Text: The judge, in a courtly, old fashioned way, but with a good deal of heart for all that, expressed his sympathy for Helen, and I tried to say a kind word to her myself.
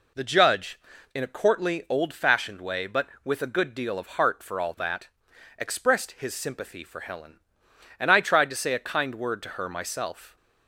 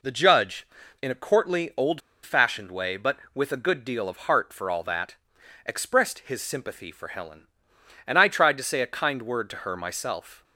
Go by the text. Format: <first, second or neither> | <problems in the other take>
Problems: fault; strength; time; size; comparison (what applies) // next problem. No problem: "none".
first | pauses between "old" and "fashioned"; slight; at 2.0 s; 0.22 s long